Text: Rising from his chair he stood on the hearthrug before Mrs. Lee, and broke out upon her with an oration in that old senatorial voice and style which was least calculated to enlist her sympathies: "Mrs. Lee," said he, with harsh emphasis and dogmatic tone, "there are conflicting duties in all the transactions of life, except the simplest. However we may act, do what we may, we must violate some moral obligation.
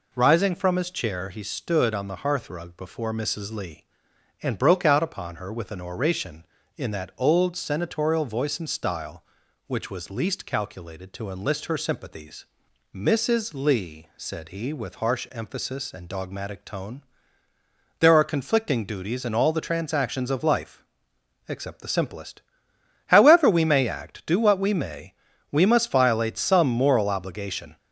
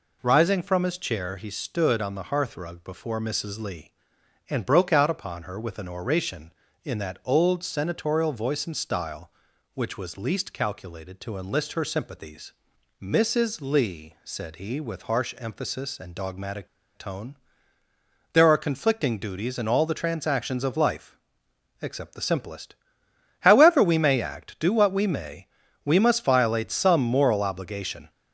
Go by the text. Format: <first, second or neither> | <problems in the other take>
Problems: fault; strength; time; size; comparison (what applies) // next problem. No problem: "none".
first | pauses between "dogmatic" and "tone"; slight; at 16.6 s; 0.27 s long